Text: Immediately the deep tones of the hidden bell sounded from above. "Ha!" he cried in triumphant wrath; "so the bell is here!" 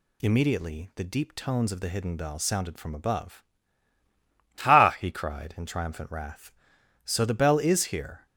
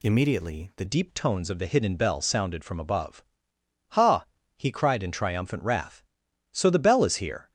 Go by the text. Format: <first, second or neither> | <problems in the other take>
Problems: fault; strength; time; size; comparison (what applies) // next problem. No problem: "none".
first | changes voice at "deep"; from 0.8 s on; 6.7 s long